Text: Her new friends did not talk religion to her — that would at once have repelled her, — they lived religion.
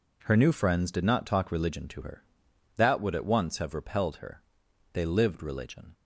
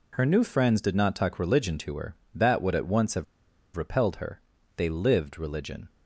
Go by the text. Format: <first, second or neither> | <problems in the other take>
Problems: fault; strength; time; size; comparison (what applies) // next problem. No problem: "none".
first | pauses between "have" and "repelled"; noticeable; at 3.2 s; 0.51 s long